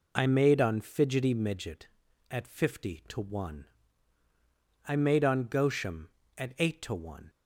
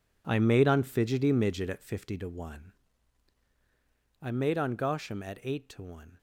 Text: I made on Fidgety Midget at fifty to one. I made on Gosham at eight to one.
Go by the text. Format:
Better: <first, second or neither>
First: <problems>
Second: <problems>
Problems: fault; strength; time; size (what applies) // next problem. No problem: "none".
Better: first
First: none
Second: gets quieter; strong; throughout; 12.5 dB